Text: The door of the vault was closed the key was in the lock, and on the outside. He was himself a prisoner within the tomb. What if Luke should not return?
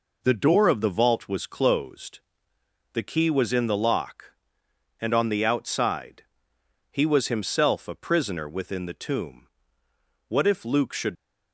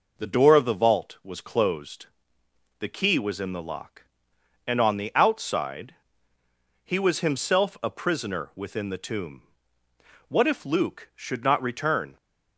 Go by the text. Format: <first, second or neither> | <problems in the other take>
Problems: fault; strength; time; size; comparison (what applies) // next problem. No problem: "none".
second | pauses between "closed" and "the"; noticeable; at 2.1 s; 0.74 s long; noticeable in the second // stops before "not return"; at 11.1 s